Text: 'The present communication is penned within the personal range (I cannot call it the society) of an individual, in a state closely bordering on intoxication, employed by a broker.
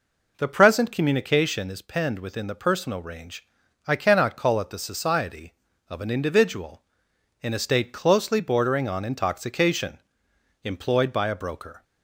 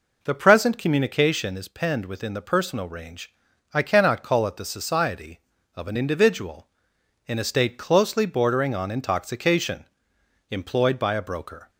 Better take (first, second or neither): neither